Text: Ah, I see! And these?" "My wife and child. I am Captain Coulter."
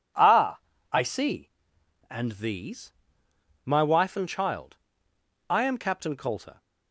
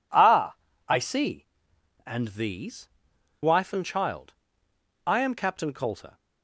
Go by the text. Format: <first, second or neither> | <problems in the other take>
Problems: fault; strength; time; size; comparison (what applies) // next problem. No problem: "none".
first | skips "My"; at 3.1 s